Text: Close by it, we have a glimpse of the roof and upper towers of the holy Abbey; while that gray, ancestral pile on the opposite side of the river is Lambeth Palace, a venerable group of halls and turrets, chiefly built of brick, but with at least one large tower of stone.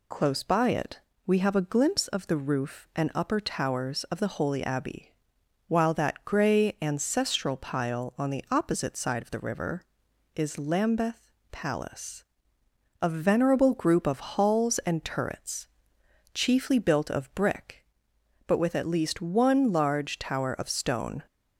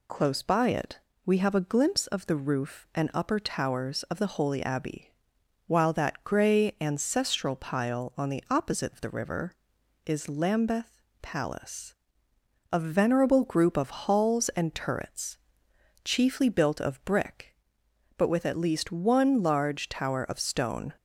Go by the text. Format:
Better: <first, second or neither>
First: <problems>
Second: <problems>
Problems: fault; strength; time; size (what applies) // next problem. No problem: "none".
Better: first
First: pauses between "Lambeth" and "Palace"; slight; at 11.2 s; 0.22 s long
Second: skips "side"; at 8.9 s // pauses between "Lambeth" and "Palace"; slight; at 11.0 s; 0.22 s long